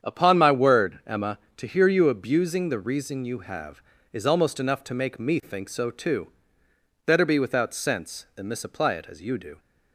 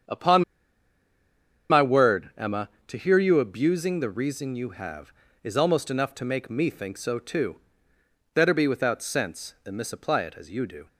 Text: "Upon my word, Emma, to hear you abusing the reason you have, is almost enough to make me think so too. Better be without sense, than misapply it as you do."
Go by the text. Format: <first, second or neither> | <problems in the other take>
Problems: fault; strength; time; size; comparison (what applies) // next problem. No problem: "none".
first | starts louder than the rest; strong; until 2.4 s; 8 dB; strong in the first // pauses between "Upon" and "my"; strong; at 0.4 s; 1.2 s long